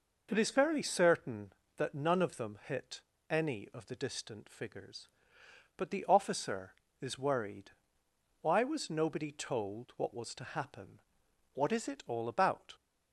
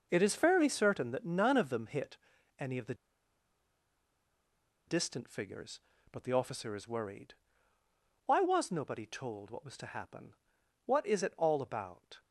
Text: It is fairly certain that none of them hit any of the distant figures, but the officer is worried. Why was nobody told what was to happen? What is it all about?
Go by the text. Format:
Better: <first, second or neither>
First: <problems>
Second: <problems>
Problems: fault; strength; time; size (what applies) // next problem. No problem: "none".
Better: first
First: pauses between "hit" and "any"; slight; at 3.0 s; 0.30 s long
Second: pauses between "hit" and "any"; at 2.1 s; 0.42 s long // pauses between "the" and "distant"; strong; at 2.9 s; 1.9 s long